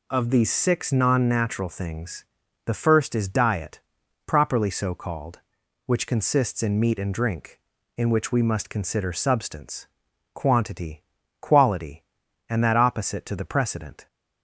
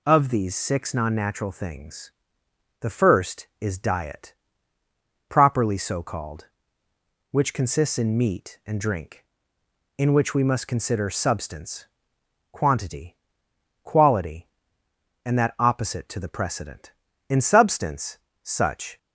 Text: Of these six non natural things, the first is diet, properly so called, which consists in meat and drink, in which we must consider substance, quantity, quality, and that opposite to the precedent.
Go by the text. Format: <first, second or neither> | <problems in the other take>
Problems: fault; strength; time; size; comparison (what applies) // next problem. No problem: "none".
first | goes on to say "In substance such"; strong; from 17.2 s on; 1.6 s long